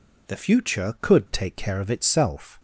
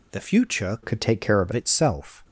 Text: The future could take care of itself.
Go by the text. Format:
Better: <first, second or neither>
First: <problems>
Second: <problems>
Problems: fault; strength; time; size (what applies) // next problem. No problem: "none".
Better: first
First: none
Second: changes voice from "could" to "of"; from 0.8 to 1.5 s; 0.7 s long